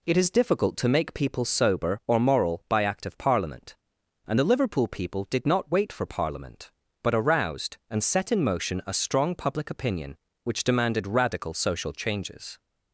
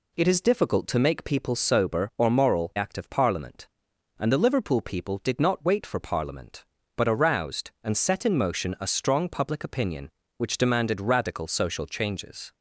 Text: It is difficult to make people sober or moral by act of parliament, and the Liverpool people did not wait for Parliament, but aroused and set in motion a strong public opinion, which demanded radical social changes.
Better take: first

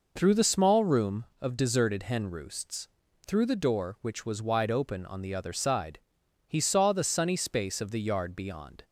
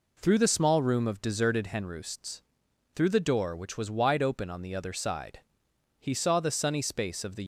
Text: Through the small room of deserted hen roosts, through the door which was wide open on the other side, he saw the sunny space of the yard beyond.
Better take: first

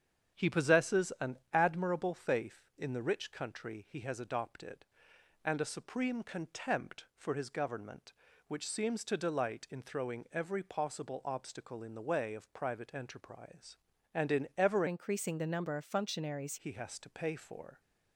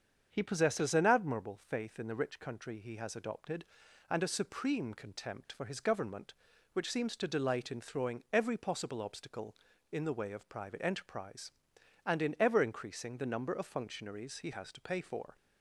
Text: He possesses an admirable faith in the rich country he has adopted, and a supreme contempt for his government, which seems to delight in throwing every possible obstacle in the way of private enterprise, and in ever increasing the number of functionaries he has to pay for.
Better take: second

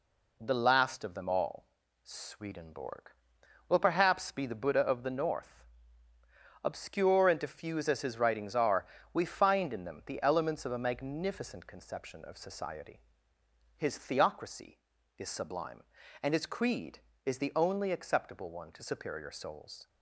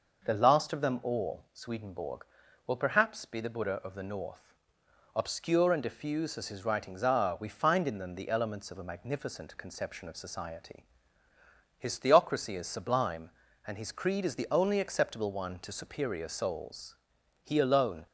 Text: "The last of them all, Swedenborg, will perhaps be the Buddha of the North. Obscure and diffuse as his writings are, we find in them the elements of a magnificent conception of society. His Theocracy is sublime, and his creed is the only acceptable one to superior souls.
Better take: first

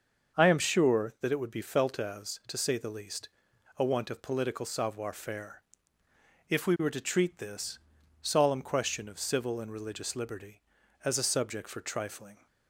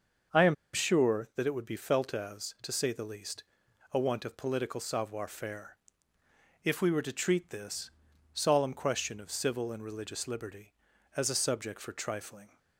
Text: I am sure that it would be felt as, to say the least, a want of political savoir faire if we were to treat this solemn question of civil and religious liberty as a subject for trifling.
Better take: first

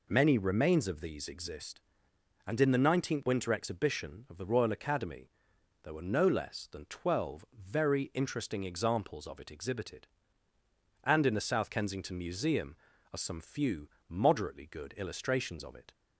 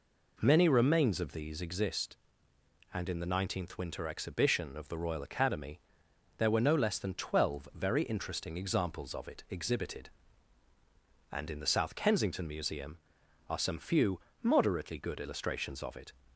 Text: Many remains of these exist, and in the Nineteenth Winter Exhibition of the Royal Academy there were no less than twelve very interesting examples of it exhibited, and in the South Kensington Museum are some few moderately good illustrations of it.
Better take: neither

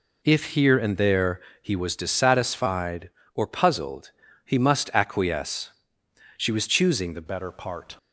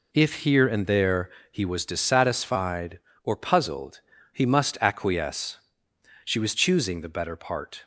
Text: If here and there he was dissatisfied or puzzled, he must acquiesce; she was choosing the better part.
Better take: second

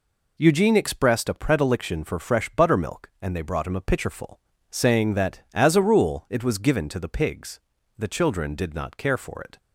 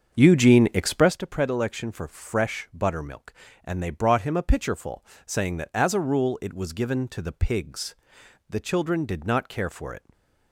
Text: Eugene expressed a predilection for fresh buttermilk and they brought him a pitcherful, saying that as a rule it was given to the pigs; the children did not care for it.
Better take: first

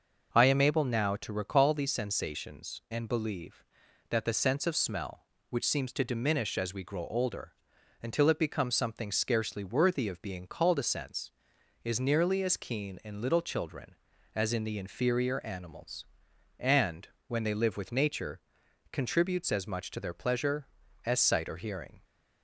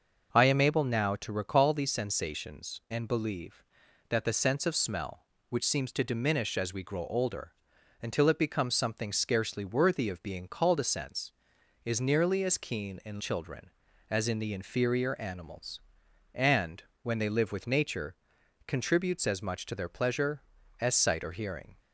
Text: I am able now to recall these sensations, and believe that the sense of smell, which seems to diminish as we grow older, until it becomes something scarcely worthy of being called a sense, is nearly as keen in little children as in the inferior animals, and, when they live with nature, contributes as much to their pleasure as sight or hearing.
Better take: first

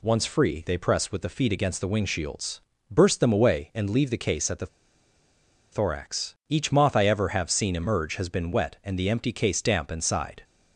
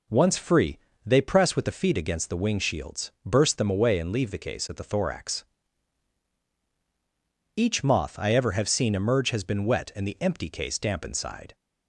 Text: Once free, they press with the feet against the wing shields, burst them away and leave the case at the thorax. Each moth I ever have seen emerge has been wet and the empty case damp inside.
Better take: second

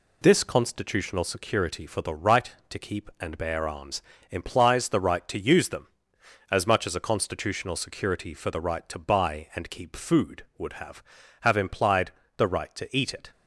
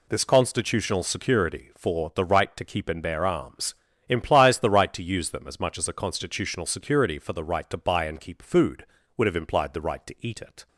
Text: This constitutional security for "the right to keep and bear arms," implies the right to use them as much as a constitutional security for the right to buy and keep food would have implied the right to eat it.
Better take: second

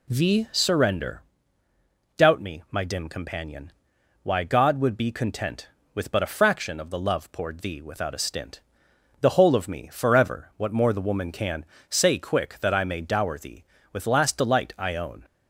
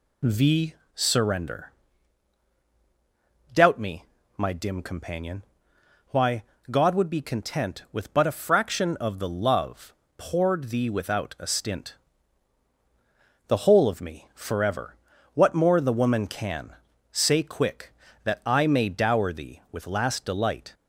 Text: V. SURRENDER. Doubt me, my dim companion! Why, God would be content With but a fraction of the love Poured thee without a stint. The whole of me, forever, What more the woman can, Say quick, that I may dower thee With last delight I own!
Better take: first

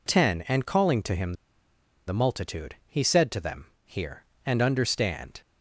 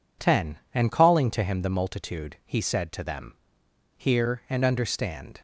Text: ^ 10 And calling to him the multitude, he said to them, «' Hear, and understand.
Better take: second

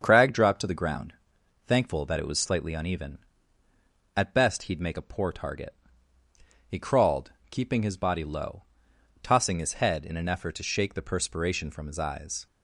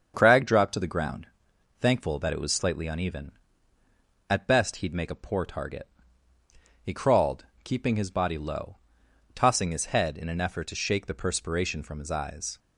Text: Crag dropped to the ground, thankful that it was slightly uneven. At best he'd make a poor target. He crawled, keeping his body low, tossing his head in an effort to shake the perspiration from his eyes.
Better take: neither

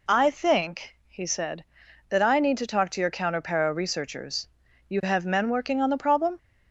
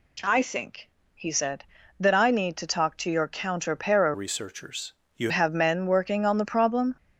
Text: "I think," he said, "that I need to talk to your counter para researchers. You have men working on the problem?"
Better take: first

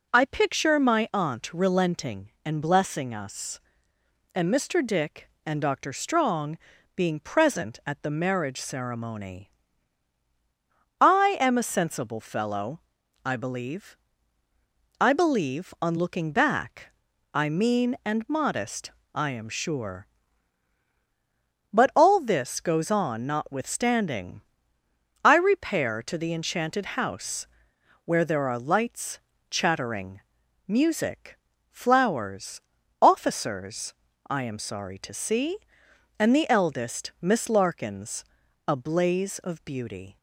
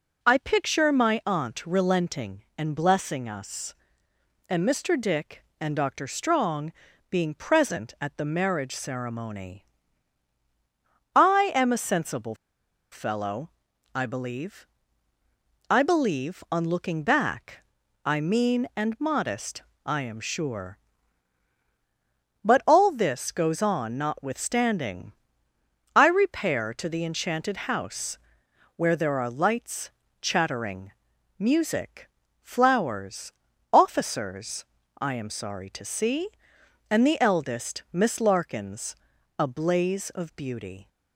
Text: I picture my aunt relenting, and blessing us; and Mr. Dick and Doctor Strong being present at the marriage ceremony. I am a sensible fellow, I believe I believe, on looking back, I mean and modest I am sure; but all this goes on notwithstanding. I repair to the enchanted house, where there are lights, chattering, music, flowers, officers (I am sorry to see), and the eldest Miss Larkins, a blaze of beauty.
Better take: first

